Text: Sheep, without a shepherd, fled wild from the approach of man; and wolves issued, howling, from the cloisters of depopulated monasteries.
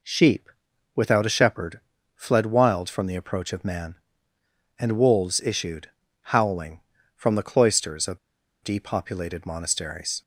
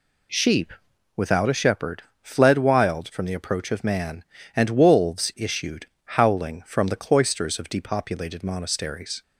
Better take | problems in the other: second | pauses between "of" and "depopulated"; at 8.1 s; 0.44 s long

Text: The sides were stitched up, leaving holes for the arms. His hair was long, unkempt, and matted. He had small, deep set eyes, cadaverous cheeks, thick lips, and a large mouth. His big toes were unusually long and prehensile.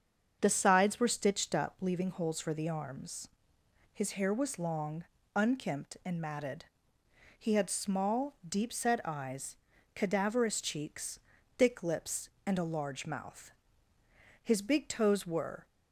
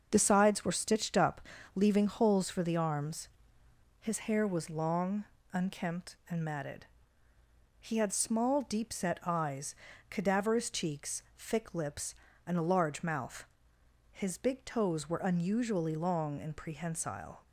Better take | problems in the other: second | starts louder than the rest; until 1.4 s; 7 dB; also in the second // stops before "unusually long and prehensile"; at 15.6 s

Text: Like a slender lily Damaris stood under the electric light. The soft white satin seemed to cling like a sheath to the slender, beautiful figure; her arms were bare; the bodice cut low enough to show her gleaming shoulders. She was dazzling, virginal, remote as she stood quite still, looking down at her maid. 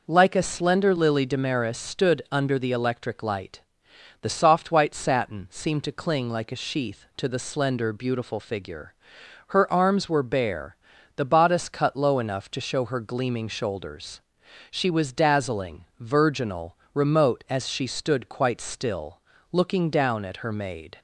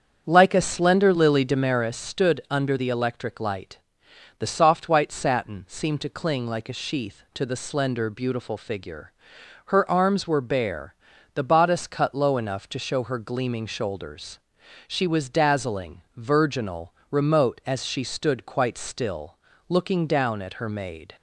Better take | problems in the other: first | starts louder than the rest; strong; until 1.9 s; 7.5 dB

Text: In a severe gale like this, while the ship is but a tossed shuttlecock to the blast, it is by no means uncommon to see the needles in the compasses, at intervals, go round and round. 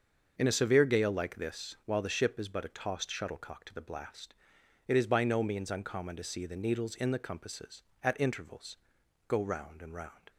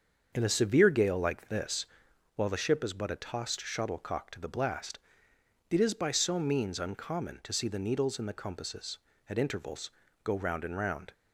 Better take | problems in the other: first | starts louder than the rest; until 1.3 s; 7 dB; also in the first // says "so" for "no"; at 6.1 s

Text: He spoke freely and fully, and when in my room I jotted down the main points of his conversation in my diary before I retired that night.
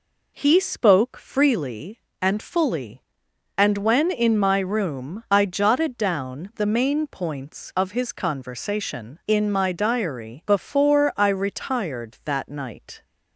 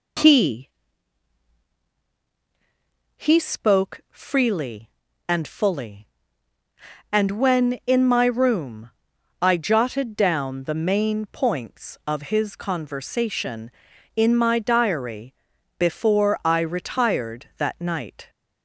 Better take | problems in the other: first | says "He" twice; at 3.1 s // pauses between "room" and "I"; noticeable; at 8.8 s; 0.50 s long // pauses between "diary" and "before"; at 15.3 s; 0.44 s long

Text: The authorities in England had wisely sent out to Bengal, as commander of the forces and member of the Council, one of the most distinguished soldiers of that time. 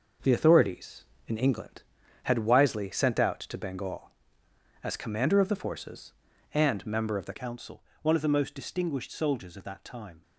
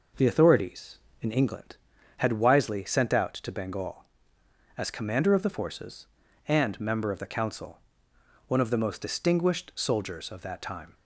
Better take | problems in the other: second | changes voice at "Council"; from 7.3 s on; 2.9 s long

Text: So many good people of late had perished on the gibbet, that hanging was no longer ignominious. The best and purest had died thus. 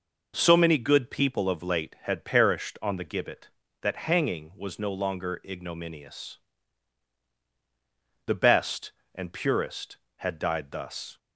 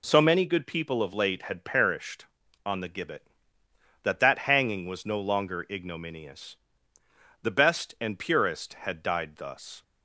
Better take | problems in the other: first | says "that" twice; at 4.1 s

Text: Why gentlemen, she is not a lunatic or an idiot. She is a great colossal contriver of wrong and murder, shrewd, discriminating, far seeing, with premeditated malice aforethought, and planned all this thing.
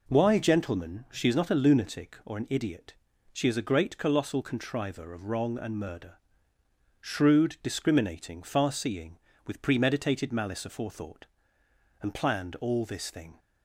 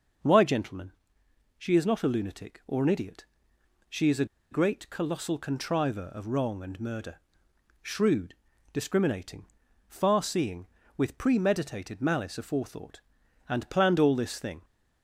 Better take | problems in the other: first | pauses between "a" and "great"; slight; at 4.2 s; 0.26 s long

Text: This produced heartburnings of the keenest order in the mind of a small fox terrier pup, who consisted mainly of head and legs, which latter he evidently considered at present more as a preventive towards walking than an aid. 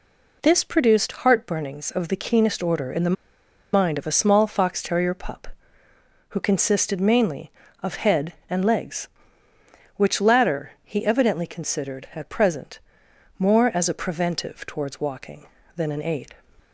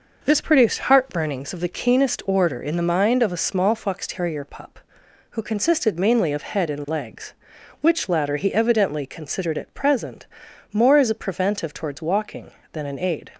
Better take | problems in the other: second | pauses between "the" and "mind"; noticeable; at 3.1 s; 0.60 s long // pauses between "present" and "more"; noticeable; at 12.7 s; 0.58 s long; noticeable in the second

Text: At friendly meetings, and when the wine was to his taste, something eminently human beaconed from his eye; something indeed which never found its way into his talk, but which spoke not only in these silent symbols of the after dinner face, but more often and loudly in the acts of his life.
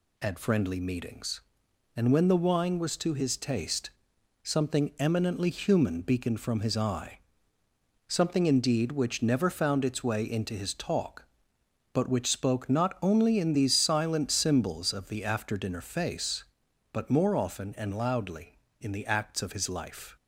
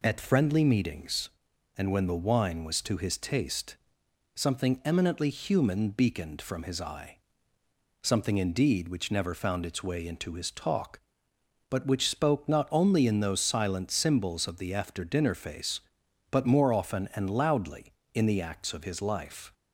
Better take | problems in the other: first | says "those" for "these"; at 13.2 s

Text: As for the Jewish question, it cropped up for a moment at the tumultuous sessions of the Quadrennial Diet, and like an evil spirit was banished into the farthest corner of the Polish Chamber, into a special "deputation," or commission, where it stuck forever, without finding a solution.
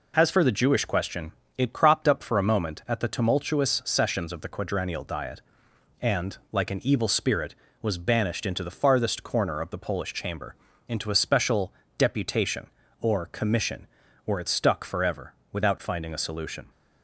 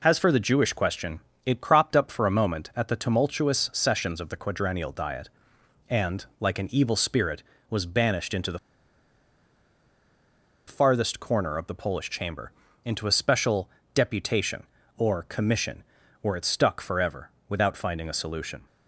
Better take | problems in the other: first | pauses between "and" and "like"; slight; at 6.2 s; 0.16 s long; slight in the first // pauses between "the" and "farthest"; strong; at 8.5 s; 2.0 s long // pauses between "special" and "deputation"; slight; at 13.6 s; 0.24 s long; slight in the first

